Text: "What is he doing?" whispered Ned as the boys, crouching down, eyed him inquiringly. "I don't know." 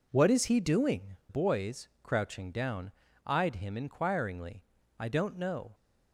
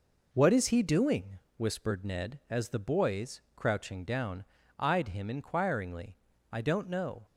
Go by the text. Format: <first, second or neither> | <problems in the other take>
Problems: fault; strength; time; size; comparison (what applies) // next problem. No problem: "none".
second | skips "whispered Ned as the"; at 1.2 s